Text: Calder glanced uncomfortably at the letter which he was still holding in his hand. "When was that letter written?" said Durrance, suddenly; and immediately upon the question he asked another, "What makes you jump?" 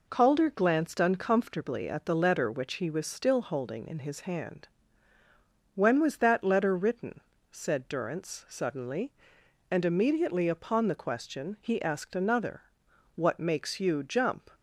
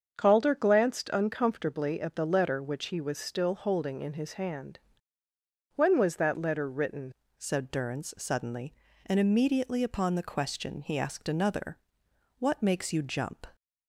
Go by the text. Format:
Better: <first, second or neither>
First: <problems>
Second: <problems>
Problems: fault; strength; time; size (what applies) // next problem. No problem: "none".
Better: first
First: none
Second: starts louder than the rest; strong; until 1.1 s; 7 dB // changes voice at "said"; from 7.3 s on; 6.1 s long